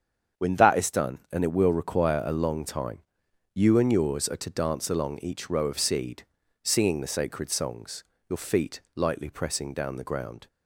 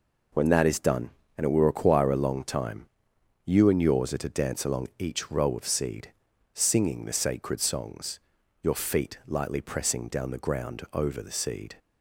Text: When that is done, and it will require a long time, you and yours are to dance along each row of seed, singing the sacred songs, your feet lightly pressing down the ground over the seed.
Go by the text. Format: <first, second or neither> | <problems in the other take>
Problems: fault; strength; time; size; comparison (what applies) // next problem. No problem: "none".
second | starts louder than the rest; strong; until 1.4 s; 7.5 dB // pauses between "feet" and "lightly"; slight; at 8.8 s; 0.16 s long // stops before "over the seed"; at 10.4 s